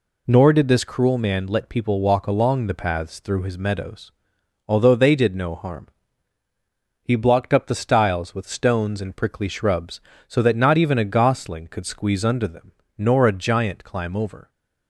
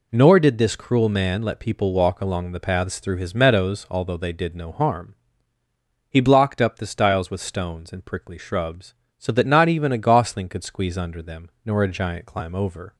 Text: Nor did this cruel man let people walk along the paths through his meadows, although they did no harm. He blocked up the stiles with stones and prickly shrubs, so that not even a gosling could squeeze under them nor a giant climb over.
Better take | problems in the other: neither | pauses between "them" and "nor"; slight; the same in both

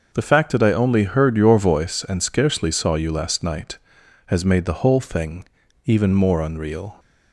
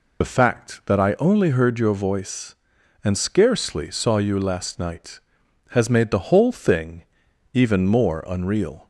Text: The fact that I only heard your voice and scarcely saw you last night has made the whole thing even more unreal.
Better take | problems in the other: first | loses the start of "The"; at 0.2 s; 35 ms // pauses between "thing" and "even"; noticeable; at 7.0 s; 0.50 s long; also in the first

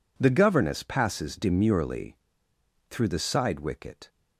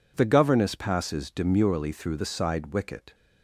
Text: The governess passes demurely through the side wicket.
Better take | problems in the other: second | pauses between "demurely" and "through"; noticeable; at 2.1 s; 0.71 s long

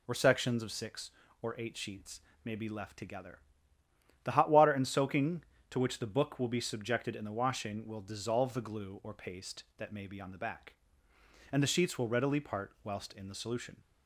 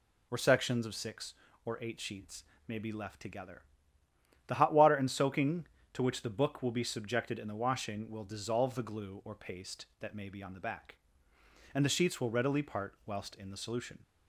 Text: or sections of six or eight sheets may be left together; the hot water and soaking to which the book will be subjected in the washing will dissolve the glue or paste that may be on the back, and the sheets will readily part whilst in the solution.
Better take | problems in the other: neither | pauses between "sheets" and "may"; slight; the same in both

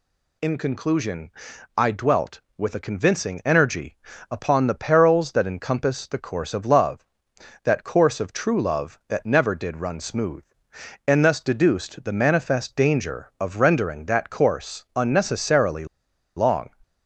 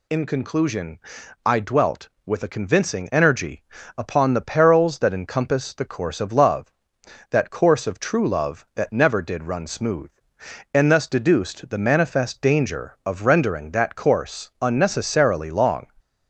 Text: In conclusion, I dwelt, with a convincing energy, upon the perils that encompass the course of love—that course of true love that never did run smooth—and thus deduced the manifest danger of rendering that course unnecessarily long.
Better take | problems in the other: second | pauses between "unnecessarily" and "long"; noticeable; at 15.8 s; 0.51 s long

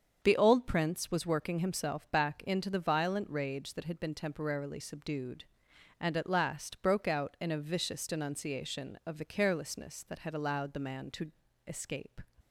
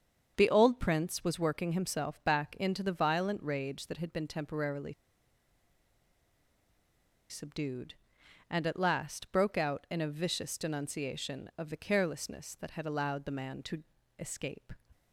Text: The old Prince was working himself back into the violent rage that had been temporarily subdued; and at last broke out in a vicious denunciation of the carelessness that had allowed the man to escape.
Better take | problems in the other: first | starts louder than the rest; strong; until 1.3 s; 7 dB; strong in the first // pauses between "temporarily" and "subdued"; strong; at 4.9 s; 2.3 s long // pauses between "to" and "escape"; slight; at 13.8 s; 0.36 s long; slight in the first

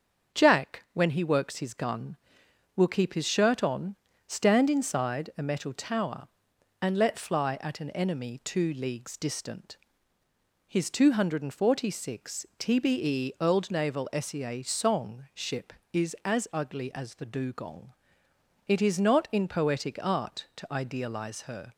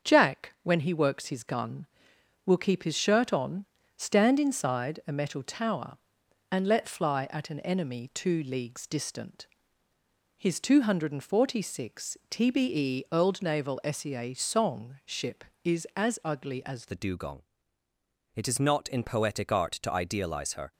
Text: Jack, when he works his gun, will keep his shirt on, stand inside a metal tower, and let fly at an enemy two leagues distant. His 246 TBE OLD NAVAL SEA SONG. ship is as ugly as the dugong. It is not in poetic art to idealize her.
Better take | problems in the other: first | starts louder than the rest; until 1.1 s; 7 dB; also in the first // changes voice at "the"; from 16.8 s on; 3.9 s long

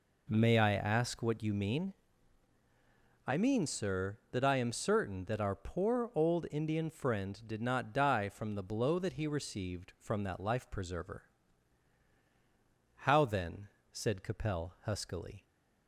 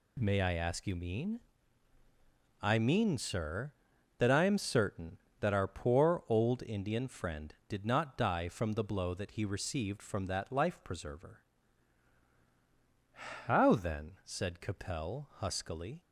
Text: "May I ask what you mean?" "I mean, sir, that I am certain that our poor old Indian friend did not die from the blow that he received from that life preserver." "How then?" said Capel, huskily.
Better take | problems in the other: first | skips "what"; at 0.8 s

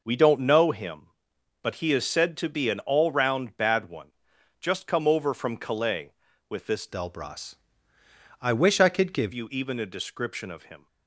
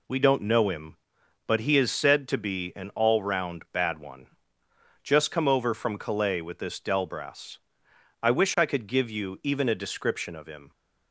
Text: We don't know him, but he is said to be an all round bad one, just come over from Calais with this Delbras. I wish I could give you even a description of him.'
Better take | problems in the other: second | changes voice from "Delbras" to "give"; from 6.8 to 9.3 s; 2.5 s long

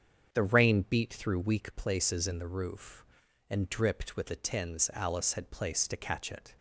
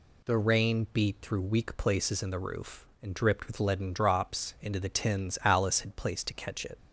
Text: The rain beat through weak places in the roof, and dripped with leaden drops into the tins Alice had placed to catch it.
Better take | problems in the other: second | starts louder than the rest; strong; until 1.3 s; 7.5 dB // skips "leaden drops into"; at 4.2 s

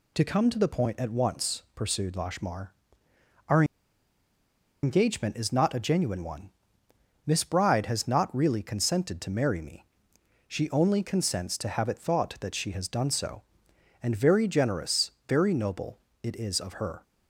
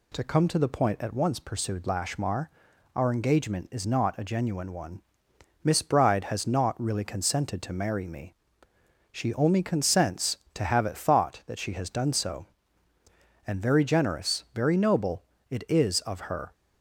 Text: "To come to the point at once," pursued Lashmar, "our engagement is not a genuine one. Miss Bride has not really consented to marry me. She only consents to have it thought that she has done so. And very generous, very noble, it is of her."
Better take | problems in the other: second | pauses between "our" and "engagement"; at 3.6 s; 1.1 s long

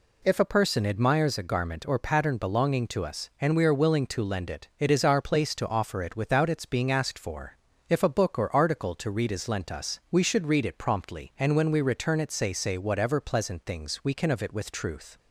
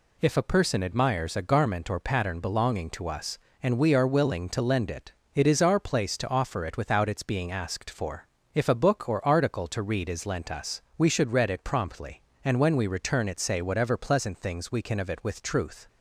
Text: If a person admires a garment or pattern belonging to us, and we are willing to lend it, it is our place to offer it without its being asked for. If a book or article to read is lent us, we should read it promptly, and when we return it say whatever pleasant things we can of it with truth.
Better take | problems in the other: second | says "say" twice; at 12.5 s

